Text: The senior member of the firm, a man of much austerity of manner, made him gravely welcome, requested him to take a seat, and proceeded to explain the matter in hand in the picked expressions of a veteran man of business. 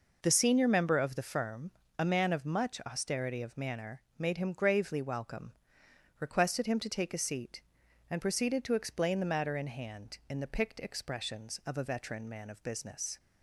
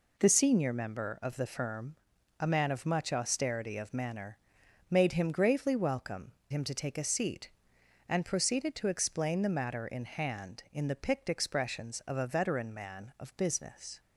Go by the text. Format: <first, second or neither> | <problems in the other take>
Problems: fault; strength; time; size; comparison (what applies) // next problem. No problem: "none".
first | skips "requested"; at 6.4 s